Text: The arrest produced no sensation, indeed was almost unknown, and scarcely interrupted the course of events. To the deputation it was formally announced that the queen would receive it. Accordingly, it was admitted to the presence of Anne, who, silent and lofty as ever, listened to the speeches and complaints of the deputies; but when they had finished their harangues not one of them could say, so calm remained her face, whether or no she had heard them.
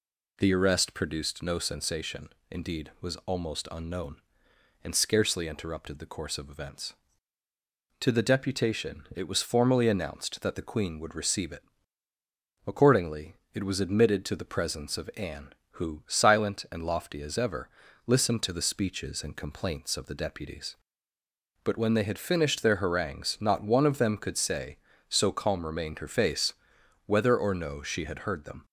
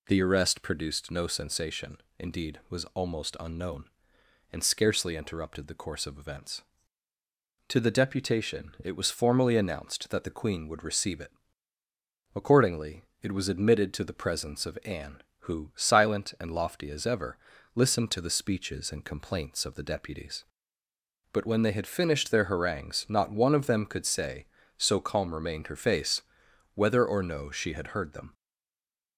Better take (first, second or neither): first